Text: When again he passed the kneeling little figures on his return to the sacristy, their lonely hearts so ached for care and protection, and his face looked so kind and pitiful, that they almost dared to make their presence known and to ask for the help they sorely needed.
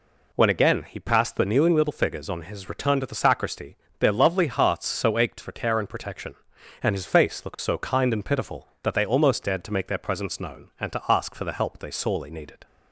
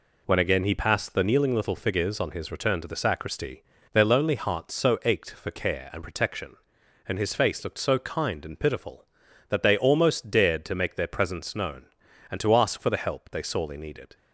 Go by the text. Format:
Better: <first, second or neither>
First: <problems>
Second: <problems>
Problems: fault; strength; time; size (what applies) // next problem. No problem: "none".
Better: second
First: says "lovely" for "lonely"; at 4.1 s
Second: none